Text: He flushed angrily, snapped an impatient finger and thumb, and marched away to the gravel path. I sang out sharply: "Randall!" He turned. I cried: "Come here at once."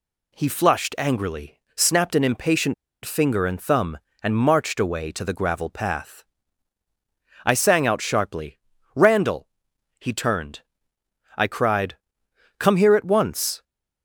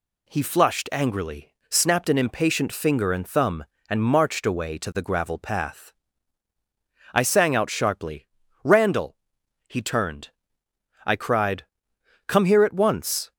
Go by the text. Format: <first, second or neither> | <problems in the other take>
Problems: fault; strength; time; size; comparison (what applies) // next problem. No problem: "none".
second | pauses between "impatient" and "finger"; slight; at 2.7 s; 0.30 s long